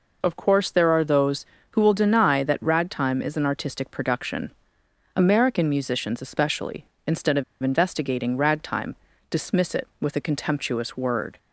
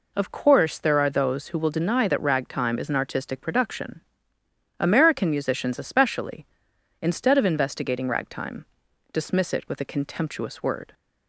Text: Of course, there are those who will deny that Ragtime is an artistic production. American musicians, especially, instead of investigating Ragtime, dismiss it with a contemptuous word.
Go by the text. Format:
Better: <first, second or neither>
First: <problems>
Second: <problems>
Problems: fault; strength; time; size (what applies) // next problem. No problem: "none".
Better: second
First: pauses between "of" and "investigating"; slight; at 7.4 s; 0.19 s long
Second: none